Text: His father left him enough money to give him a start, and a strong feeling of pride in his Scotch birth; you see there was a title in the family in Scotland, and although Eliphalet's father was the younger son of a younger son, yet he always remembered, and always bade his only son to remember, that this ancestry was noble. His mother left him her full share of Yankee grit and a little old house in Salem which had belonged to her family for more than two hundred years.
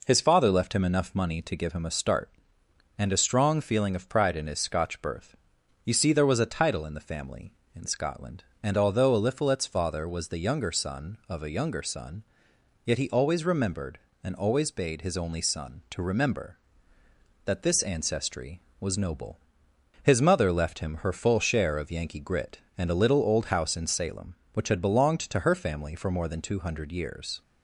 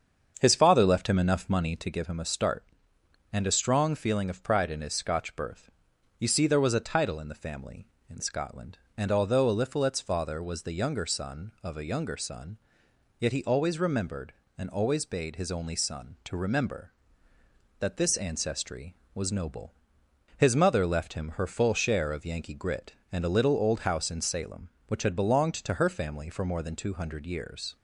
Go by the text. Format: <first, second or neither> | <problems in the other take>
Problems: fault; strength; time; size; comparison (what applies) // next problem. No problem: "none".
first | starts louder than the rest; until 1.9 s; 7 dB